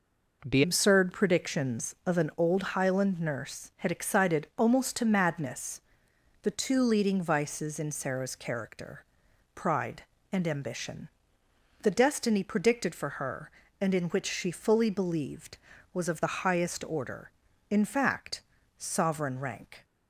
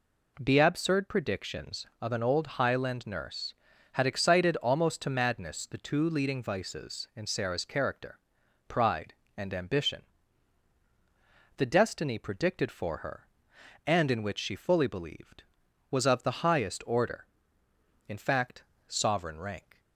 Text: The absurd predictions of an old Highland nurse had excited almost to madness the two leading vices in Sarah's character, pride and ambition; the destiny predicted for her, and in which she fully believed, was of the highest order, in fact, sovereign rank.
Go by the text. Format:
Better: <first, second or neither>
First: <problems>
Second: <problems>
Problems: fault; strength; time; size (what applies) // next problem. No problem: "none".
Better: second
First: changes voice at "absurd"; from 0.6 s on; 19.2 s long // pauses between "madness" and "the"; noticeable; at 5.8 s; 0.64 s long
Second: none